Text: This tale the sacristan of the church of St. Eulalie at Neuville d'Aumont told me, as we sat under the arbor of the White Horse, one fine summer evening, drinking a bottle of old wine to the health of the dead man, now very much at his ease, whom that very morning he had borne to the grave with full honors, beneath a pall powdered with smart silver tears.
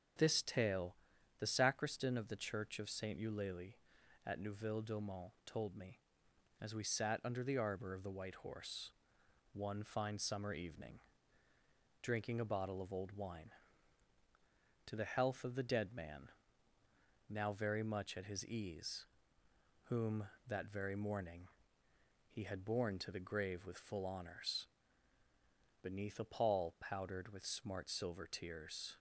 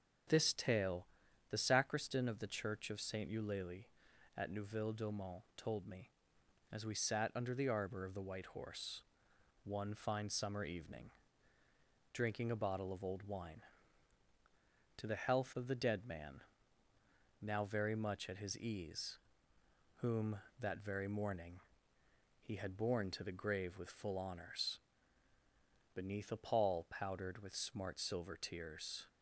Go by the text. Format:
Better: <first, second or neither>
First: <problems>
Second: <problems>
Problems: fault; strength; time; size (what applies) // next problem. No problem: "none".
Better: neither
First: starts louder than the rest; until 1.6 s; 7 dB // pauses between "tale" and "the"; at 0.9 s; 0.44 s long // pauses between "d'Aumont" and "told"; slight; at 5.2 s; 0.16 s long // pauses between "morning" and "he"; noticeable; at 21.4 s; 0.86 s long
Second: starts louder than the rest; until 1.7 s; 7 dB // pauses between "tale" and "the"; at 1.0 s; 0.44 s long // pauses between "d'Aumont" and "told"; slight; at 5.4 s; 0.16 s long // pauses between "morning" and "he"; noticeable; at 21.5 s; 0.86 s long